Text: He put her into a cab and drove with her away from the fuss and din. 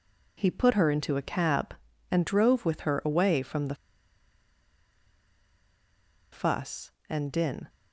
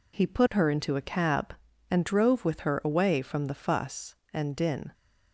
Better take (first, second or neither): second